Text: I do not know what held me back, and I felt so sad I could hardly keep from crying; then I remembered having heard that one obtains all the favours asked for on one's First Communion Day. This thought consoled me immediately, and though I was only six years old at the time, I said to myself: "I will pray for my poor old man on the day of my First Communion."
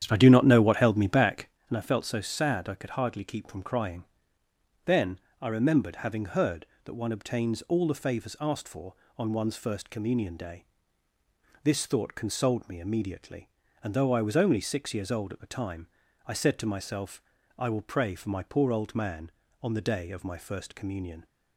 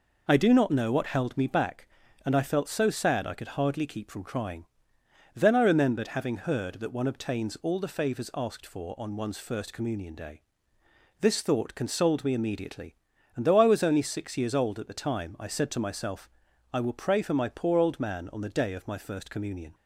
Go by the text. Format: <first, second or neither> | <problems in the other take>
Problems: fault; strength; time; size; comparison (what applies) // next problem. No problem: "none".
second | starts louder than the rest; strong; until 1.6 s; 9.5 dB // pauses between "then" and "I"; slight; at 5.1 s; 0.24 s long